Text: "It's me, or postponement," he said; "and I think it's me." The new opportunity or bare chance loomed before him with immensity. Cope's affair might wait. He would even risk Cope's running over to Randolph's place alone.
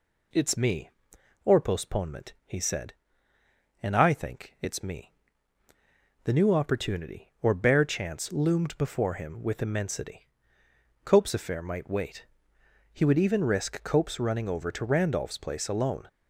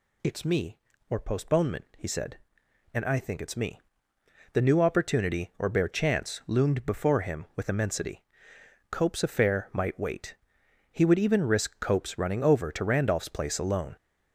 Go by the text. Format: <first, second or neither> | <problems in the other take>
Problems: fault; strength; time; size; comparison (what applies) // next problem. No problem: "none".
neither | none